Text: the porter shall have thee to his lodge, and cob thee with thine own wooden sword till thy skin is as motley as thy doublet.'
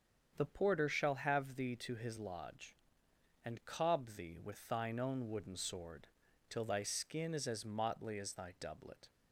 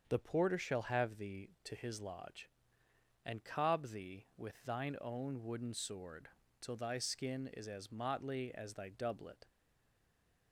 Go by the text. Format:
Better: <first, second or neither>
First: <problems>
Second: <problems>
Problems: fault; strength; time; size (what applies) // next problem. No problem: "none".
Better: first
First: starts louder than the rest; strong; until 1.3 s; 7 dB // pauses between "sword" and "till"; at 6.0 s; 0.42 s long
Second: starts louder than the rest; strong; until 1.0 s; 7 dB // pauses between "sword" and "till"; slight; at 6.2 s; 0.32 s long // stays silent after the last word; from 9.4 s on; 1.1 s long